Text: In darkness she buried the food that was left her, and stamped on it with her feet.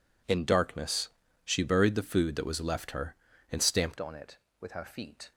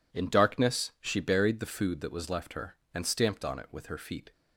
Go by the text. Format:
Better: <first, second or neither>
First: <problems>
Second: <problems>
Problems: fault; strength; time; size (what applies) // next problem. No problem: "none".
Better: second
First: pauses between "darkness" and "she"; slight; at 1.0 s; 0.34 s long // changes voice at "on"; from 3.9 s on; 1.4 s long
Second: none